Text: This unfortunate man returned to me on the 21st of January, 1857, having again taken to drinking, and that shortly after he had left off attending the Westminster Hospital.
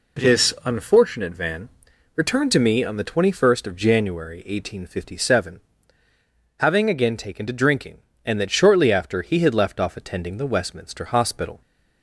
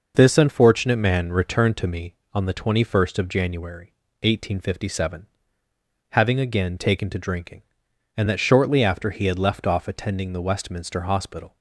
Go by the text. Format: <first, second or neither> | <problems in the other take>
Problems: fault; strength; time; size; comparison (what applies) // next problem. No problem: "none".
second | says "van" for "man"; at 1.3 s